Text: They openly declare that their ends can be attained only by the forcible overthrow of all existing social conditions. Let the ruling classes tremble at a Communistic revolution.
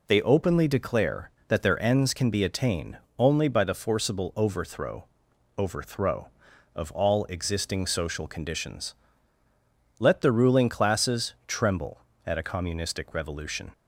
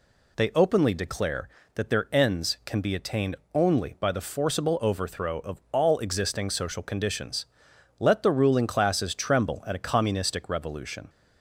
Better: second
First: pauses between "attained" and "only"; slight; at 2.9 s; 0.22 s long // says "overthrow" twice; at 5.5 s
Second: pauses between "attained" and "only"; slight; at 3.3 s; 0.16 s long

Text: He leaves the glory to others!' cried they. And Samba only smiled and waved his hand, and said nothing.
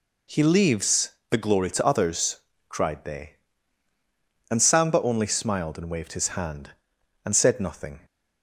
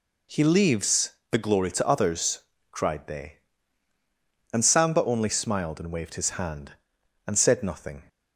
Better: neither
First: pauses between "leaves" and "the"; slight; at 1.1 s; 0.18 s long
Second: pauses between "leaves" and "the"; slight; at 1.1 s; 0.18 s long

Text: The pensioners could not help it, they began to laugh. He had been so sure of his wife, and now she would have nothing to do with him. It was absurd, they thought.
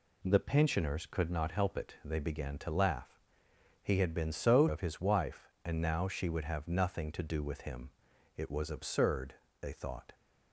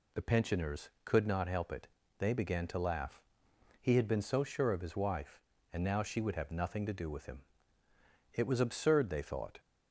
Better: second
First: skips "sure"; at 4.6 s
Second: none

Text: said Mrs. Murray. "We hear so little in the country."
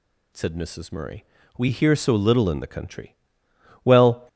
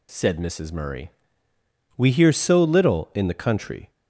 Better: second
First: goes on to say "Well"; slight; from 3.8 s on; 0.44 s long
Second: none

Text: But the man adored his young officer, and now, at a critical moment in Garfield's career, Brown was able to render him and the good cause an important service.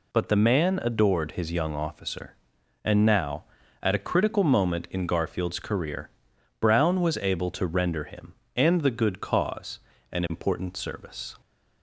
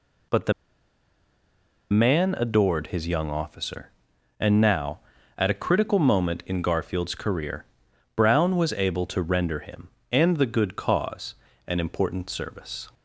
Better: first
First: pauses between "cause" and "an"; slight; at 9.7 s; 0.32 s long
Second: pauses between "the" and "man"; strong; at 0.5 s; 1.3 s long // pauses between "cause" and "an"; slight; at 11.3 s; 0.32 s long

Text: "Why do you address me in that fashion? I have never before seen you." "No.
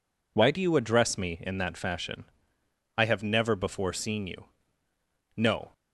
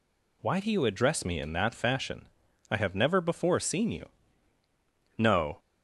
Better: neither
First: none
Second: none

